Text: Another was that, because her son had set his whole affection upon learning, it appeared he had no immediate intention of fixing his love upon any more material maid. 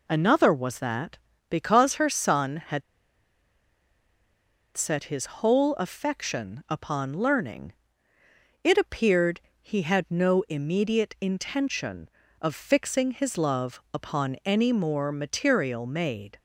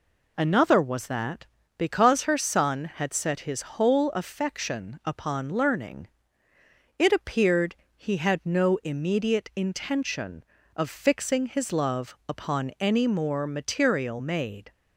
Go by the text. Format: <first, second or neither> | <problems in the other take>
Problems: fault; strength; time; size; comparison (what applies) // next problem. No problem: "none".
second | pauses between "had" and "set"; strong; at 2.8 s; 1.9 s long // pauses between "appeared" and "he"; slight; at 9.4 s; 0.20 s long; slight in the second